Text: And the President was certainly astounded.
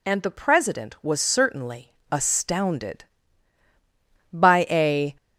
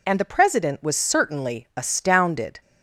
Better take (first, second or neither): second